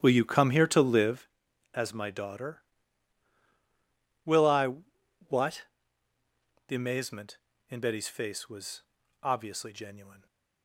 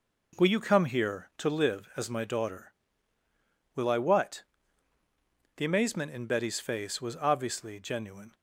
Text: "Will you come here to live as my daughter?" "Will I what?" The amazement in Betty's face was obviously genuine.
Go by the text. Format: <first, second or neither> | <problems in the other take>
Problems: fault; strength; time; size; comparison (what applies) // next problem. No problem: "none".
second | starts louder than the rest; strong; until 1.3 s; 11 dB // pauses between "I" and "what"; noticeable; at 4.7 s; 0.54 s long // pauses between "was" and "obviously"; at 8.8 s; 0.40 s long